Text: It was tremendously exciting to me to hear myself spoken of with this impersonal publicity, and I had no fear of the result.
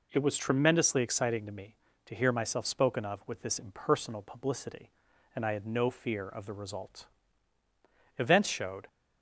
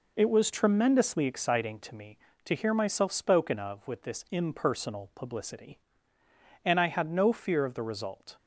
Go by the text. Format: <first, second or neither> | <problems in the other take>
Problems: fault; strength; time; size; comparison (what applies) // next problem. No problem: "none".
second | goes on to say "Events showed"; noticeable; from 8.1 s on; 0.70 s long